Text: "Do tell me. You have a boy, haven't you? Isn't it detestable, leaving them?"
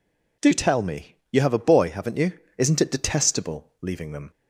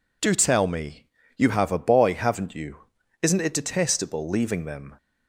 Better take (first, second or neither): neither